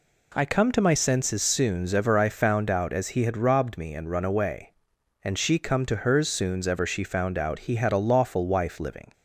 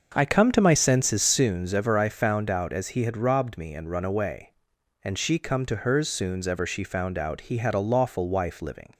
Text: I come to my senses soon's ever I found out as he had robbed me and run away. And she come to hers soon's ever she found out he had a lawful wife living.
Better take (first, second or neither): first